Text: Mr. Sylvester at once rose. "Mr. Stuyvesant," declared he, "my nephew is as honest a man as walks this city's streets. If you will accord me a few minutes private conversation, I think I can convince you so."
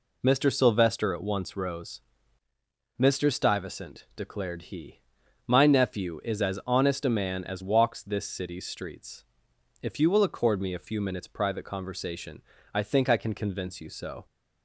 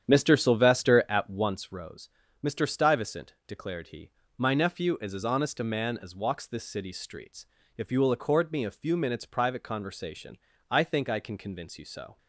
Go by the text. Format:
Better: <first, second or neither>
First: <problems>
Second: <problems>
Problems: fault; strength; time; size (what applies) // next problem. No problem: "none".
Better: first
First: none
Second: starts louder than the rest; strong; until 1.6 s; 9 dB